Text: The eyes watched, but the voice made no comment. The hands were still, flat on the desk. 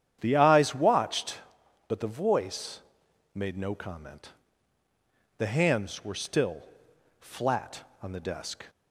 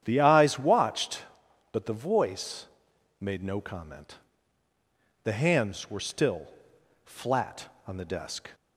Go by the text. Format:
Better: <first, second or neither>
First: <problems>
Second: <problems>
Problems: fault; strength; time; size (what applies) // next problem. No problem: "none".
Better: neither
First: starts louder than the rest; strong; until 1.2 s; 9.5 dB // pauses between "voice" and "made"; noticeable; at 2.8 s; 0.54 s long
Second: starts louder than the rest; strong; until 1.0 s; 9.5 dB // pauses between "voice" and "made"; noticeable; at 2.6 s; 0.54 s long